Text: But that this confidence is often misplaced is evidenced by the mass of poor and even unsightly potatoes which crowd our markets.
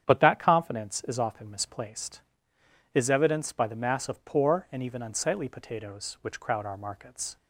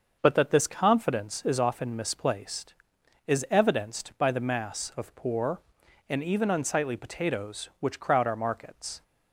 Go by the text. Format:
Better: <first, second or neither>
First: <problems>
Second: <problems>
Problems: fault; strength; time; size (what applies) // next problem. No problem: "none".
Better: second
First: starts louder than the rest; strong; until 1.1 s; 9 dB // skips "this"; at 0.3 s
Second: starts louder than the rest; until 1.2 s; 6.5 dB